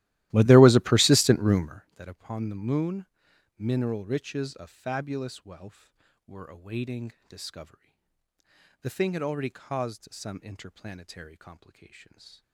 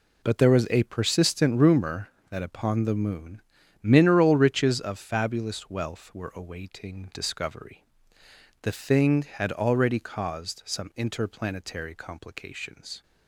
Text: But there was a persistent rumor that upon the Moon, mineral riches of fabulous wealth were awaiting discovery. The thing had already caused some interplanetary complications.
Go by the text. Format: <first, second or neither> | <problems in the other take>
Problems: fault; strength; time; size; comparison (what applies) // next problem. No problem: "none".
second | starts louder than the rest; strong; until 1.9 s; 16.5 dB // pauses between "awaiting" and "discovery"; slight; at 7.1 s; 0.16 s long